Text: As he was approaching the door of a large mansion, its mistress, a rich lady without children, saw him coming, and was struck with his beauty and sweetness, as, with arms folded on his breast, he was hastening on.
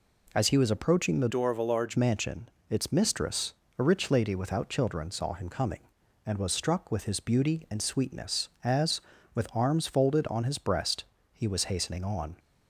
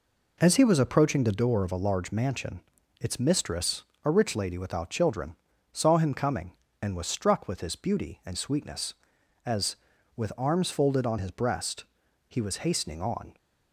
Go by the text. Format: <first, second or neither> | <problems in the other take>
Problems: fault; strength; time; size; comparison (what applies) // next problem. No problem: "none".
second | changes voice from "door" to "large"; from 1.2 to 1.9 s; 0.7 s long